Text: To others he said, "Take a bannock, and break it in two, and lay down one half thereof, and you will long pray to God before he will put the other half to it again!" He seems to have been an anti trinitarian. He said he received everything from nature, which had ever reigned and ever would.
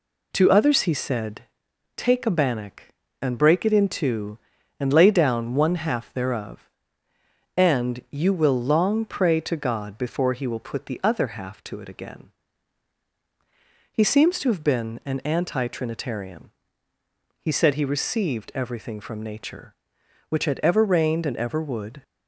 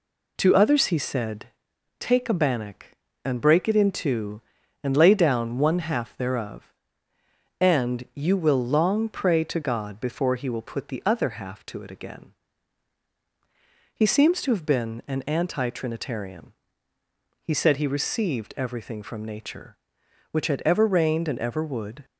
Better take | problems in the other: neither | none

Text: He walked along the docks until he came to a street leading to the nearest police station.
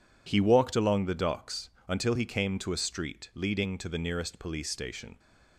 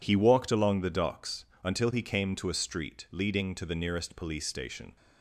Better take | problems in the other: neither | pauses between "docks" and "until"; slight; the same in both

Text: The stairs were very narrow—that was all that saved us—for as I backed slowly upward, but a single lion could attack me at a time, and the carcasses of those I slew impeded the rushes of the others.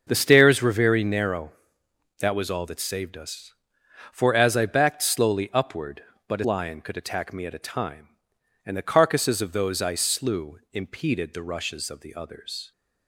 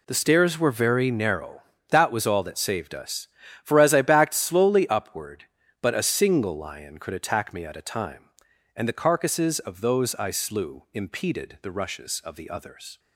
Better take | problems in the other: second | starts louder than the rest; noticeable; until 1.0 s; 6 dB // skips "single"; at 6.4 s

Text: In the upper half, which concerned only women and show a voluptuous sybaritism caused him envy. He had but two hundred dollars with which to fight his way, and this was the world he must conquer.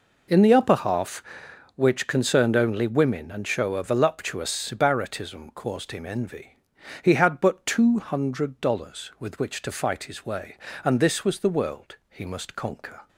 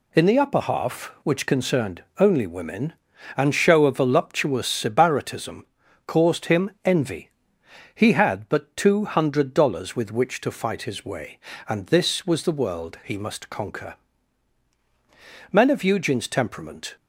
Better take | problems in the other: first | pauses between "concerned" and "only"; slight; at 2.0 s; 0.16 s long // pauses between "sybaritism" and "caused"; at 5.6 s; 0.42 s long // goes on to say "Men of Eugene's temperament"; from 15.5 s on; 1.4 s long

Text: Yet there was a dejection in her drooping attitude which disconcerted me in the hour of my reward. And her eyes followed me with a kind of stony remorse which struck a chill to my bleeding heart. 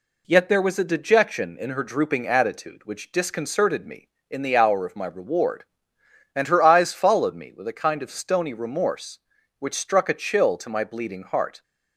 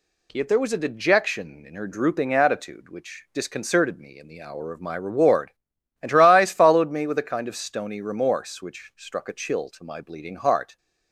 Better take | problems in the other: neither | none

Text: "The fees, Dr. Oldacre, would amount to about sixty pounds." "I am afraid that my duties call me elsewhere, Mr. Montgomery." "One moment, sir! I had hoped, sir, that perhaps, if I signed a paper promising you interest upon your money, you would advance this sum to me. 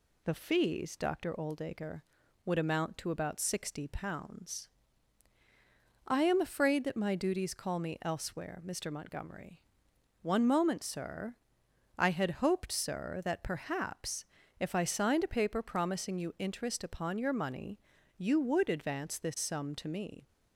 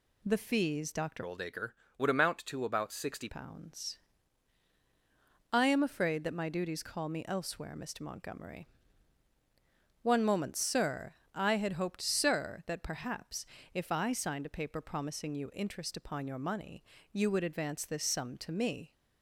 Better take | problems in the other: first | changes voice from "Oldacre" to "sixty"; from 1.2 to 3.2 s; 2.0 s long

